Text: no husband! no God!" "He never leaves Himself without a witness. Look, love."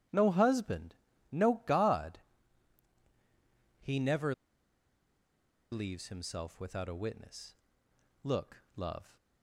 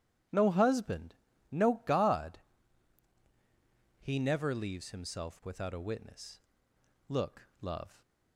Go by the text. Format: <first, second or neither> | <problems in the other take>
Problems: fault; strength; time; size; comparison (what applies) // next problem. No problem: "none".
second | pauses between "never" and "leaves"; strong; at 4.3 s; 1.3 s long